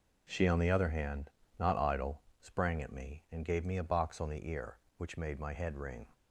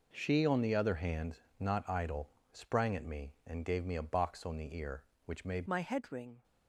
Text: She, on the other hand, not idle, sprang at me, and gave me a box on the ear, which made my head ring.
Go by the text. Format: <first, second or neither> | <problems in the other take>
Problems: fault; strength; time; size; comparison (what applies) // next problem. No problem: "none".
first | changes voice at "my"; from 5.6 s on; 0.8 s long